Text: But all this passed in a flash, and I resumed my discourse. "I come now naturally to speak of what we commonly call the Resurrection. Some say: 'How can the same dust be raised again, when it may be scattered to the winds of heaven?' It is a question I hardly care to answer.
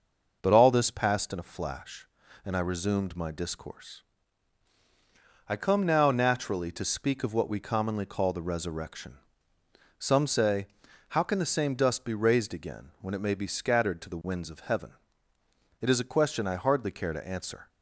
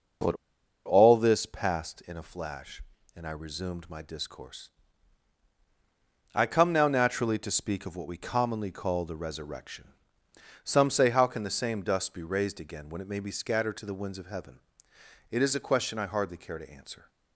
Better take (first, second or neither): first